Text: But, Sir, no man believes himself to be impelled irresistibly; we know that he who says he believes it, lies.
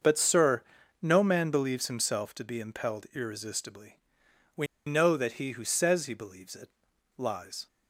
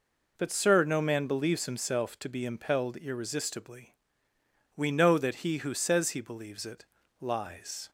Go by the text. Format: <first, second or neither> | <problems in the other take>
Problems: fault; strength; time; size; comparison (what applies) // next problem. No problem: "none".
second | starts louder than the rest; until 1.4 s; 6.5 dB // pauses between "we" and "know"; slight; at 4.6 s; 0.20 s long